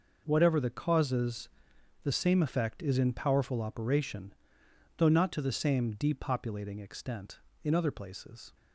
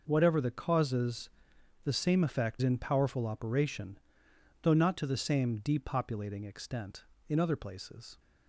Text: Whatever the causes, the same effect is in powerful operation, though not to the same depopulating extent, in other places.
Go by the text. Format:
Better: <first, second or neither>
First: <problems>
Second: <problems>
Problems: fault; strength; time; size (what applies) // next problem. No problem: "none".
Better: first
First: none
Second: skips "is"; at 2.6 s